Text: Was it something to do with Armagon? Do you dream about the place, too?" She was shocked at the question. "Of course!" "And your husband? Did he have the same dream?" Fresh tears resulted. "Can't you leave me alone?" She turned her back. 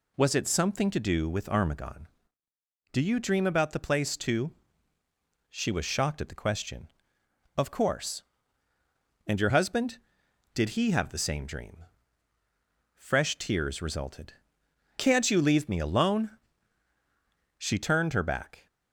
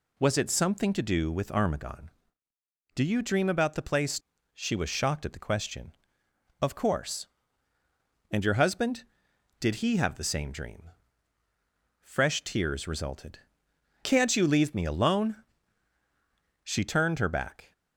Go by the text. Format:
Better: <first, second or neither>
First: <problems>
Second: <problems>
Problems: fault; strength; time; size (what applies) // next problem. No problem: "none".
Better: first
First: none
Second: skips "too"; at 4.3 s